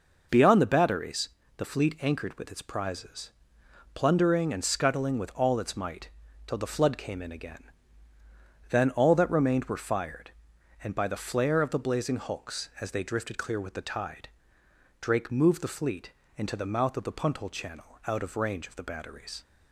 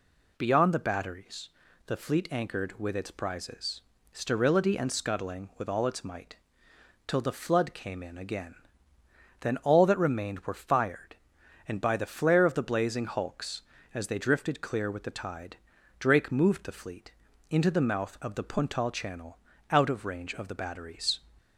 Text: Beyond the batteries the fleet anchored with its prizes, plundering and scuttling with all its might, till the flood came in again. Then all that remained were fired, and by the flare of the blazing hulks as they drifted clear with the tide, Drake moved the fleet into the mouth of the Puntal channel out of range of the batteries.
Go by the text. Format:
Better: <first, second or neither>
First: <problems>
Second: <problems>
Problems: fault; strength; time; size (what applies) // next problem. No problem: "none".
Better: first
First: pauses between "batteries" and "the"; slight; at 1.2 s; 0.28 s long // pauses between "fleet" and "into"; slight; at 16.1 s; 0.24 s long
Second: pauses between "batteries" and "the"; at 1.4 s; 0.38 s long // says "sterility" for "plundering"; at 4.1 s // pauses between "fleet" and "into"; slight; at 17.1 s; 0.36 s long // pauses between "channel" and "out"; slight; at 19.3 s; 0.34 s long